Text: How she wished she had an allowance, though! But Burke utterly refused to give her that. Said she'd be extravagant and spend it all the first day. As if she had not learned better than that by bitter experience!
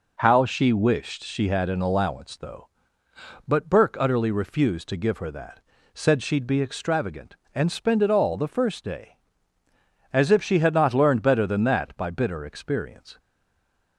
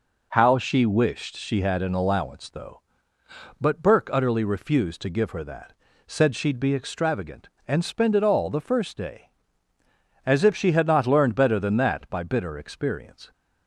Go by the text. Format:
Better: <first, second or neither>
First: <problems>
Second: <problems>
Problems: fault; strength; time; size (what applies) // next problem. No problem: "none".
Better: second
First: stays silent after the last word; slight; from 13.1 s on; 0.8 s long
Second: none